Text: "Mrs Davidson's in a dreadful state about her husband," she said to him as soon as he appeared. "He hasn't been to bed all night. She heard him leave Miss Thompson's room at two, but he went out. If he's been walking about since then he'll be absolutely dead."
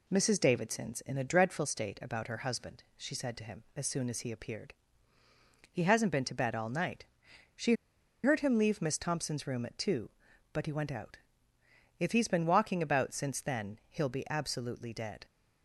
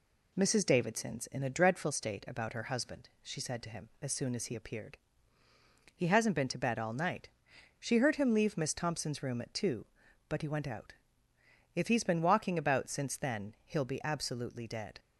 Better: second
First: pauses between "She" and "heard"; noticeable; at 7.7 s; 0.50 s long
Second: none

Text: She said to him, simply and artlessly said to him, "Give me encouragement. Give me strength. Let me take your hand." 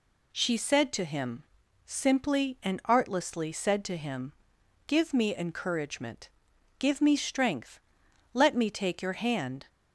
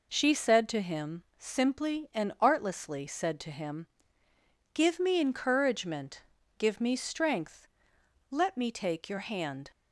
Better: neither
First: none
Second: none

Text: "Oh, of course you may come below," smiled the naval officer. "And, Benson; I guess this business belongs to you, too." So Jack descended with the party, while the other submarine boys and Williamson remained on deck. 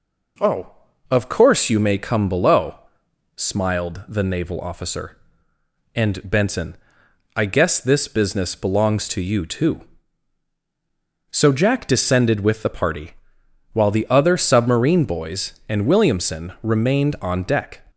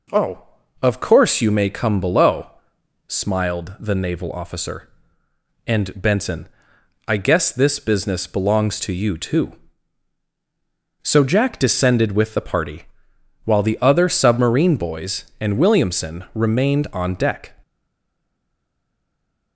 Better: first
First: none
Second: stays silent after the last word; noticeable; from 17.6 s on; 1.9 s long

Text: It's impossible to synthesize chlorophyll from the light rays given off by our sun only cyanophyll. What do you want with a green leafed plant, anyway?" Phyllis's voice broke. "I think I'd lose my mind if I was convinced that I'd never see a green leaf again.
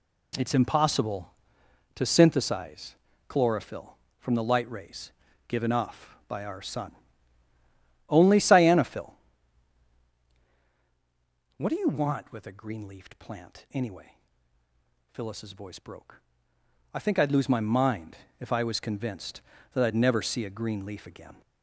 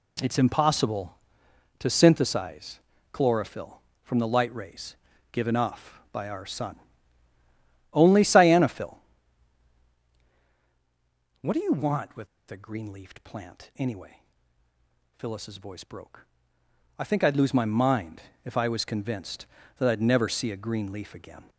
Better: first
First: pauses between "synthesize" and "chlorophyll"; slight; at 2.9 s; 0.32 s long // pauses between "rays" and "given"; slight; at 5.1 s; 0.34 s long // pauses between "sun" and "only"; at 6.9 s; 1.1 s long // pauses between "mind" and "if"; slight; at 18.1 s; 0.22 s long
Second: pauses between "synthesize" and "chlorophyll"; slight; at 2.8 s; 0.32 s long // pauses between "rays" and "given"; slight; at 4.9 s; 0.34 s long // pauses between "sun" and "only"; at 6.7 s; 1.1 s long // pauses between "with" and "a"; slight; at 12.2 s; 0.23 s long // pauses between "mind" and "if"; slight; at 18.2 s; 0.22 s long

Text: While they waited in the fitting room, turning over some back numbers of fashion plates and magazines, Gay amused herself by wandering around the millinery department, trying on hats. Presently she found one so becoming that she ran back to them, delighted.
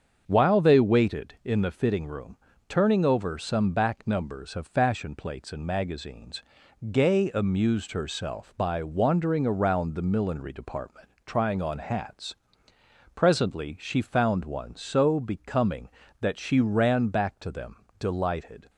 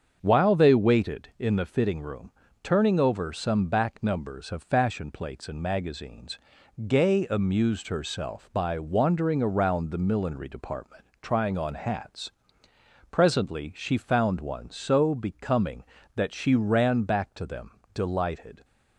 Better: neither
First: starts louder than the rest; until 1.2 s; 7 dB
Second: starts louder than the rest; until 1.2 s; 7 dB

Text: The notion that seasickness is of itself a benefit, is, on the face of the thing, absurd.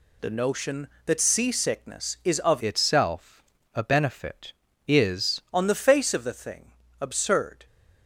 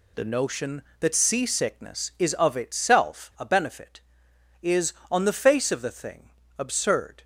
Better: second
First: changes voice from "itself" to "is"; from 2.6 to 5.3 s; 2.7 s long // pauses between "itself" and "a"; slight; at 3.4 s; 0.32 s long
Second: none

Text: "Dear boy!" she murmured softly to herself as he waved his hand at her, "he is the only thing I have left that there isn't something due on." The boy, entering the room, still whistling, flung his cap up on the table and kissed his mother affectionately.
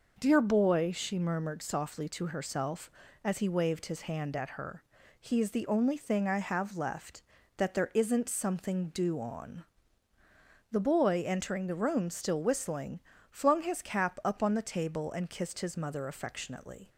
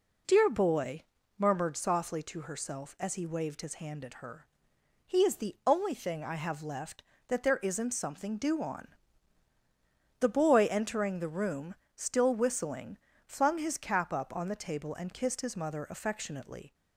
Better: first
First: none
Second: skips "she"; at 1.2 s

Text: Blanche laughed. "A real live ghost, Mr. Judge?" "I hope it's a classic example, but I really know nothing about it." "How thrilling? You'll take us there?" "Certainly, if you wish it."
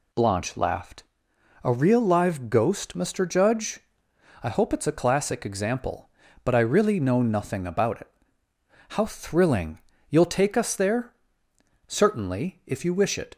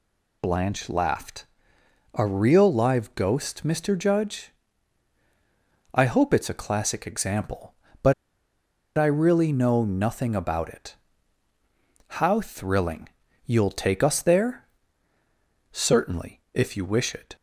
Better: first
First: none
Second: pauses between "but" and "I"; noticeable; at 8.1 s; 0.83 s long

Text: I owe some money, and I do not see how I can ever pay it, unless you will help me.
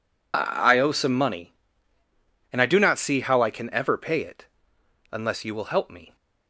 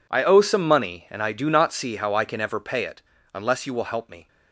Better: neither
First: none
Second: none

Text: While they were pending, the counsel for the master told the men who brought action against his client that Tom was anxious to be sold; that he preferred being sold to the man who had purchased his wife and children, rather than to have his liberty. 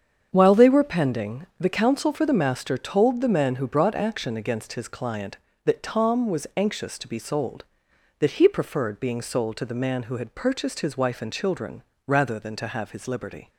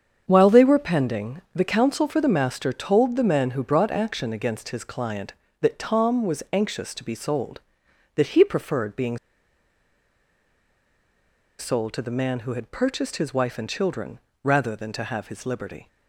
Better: first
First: starts louder than the rest; strong; until 1.3 s; 7.5 dB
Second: starts louder than the rest; strong; until 1.2 s; 7.5 dB // pauses between "being" and "sold"; strong; at 9.1 s; 2.4 s long

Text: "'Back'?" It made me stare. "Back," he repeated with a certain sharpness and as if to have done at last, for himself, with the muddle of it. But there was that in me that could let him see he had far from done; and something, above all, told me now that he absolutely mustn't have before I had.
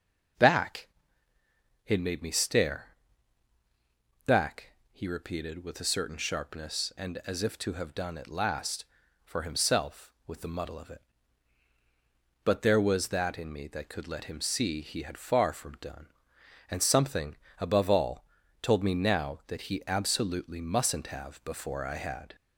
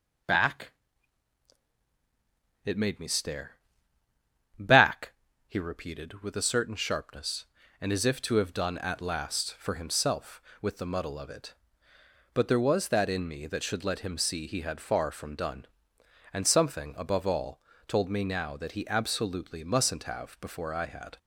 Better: first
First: none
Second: says "should" for "could"; at 13.6 s

